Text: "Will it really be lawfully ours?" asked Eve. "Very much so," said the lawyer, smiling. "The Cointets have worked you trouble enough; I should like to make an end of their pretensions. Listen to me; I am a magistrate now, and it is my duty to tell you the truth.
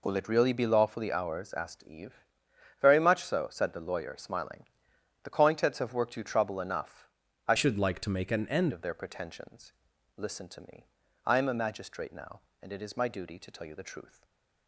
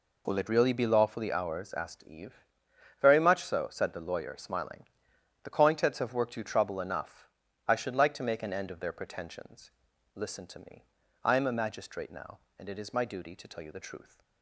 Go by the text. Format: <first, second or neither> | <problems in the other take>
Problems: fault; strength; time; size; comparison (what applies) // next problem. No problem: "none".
second | changes voice from "should" to "end"; from 7.5 to 8.7 s; 1.2 s long // stays silent after the last word; slight; from 14.0 s on; 0.6 s long